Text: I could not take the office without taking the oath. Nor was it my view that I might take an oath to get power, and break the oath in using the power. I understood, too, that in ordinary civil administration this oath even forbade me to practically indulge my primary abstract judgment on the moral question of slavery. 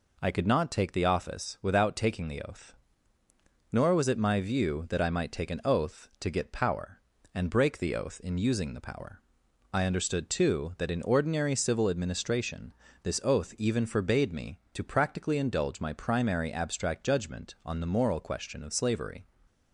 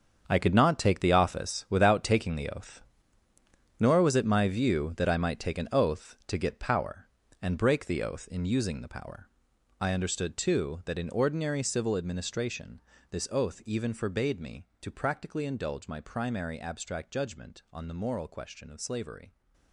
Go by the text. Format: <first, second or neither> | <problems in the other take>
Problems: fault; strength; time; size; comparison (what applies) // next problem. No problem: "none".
first | gets quieter; strong; throughout; 12 dB // pauses between "administration" and "this"; slight; at 12.7 s; 0.30 s long; slight in the first